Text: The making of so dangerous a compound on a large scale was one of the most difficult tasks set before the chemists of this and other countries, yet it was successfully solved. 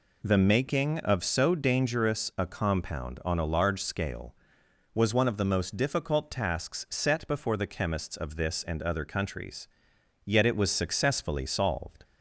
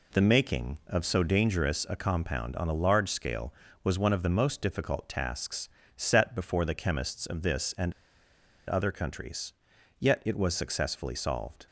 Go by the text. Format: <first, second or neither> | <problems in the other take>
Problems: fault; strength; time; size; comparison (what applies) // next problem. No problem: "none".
first | pauses between "tasks" and "set"; slight; at 5.6 s; 0.26 s long // pauses between "and" and "other"; noticeable; at 7.9 s; 0.75 s long